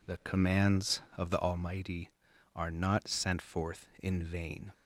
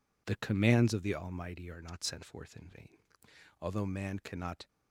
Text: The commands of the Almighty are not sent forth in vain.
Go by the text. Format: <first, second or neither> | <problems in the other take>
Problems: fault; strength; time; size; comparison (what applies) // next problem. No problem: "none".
first | goes on to say "Although man cannot"; noticeable; from 3.5 s on; 1.0 s long